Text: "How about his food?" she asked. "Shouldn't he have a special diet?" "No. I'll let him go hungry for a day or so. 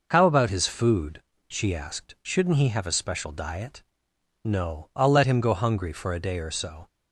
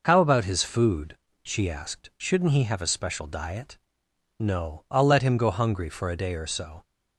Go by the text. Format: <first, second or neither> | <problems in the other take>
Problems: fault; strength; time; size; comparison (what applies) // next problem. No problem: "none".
neither | none